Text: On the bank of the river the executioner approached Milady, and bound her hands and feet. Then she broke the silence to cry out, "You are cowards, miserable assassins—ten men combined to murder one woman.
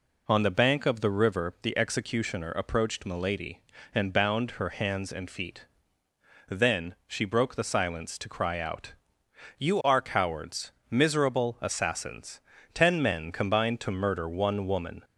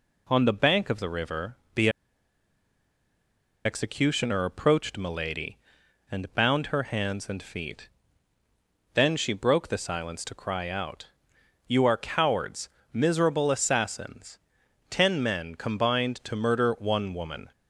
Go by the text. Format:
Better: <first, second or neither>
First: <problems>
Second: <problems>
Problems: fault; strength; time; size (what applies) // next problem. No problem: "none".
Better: first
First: none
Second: pauses between "river" and "the"; slight; at 1.5 s; 0.20 s long // pauses between "the" and "executioner"; strong; at 1.8 s; 1.7 s long